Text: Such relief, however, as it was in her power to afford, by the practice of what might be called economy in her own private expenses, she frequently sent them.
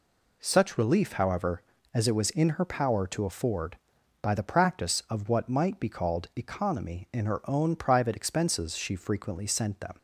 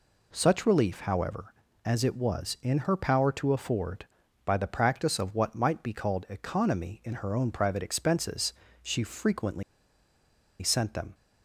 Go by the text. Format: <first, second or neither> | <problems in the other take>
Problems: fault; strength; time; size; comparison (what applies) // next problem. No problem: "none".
first | pauses between "frequently" and "sent"; at 9.6 s; 0.99 s long